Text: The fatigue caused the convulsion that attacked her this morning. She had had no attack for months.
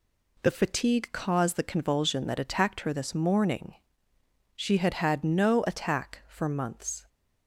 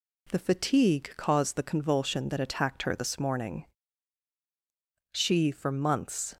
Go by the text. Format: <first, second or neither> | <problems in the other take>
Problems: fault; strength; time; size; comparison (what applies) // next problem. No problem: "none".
first | skips "had had no attack"; at 5.5 s